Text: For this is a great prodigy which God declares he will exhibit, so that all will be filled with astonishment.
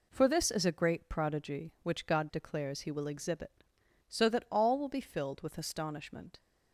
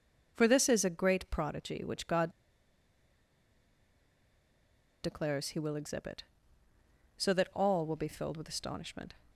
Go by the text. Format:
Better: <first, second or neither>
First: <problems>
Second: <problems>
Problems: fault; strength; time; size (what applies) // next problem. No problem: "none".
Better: first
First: none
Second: pauses between "God" and "declares"; strong; at 2.2 s; 2.7 s long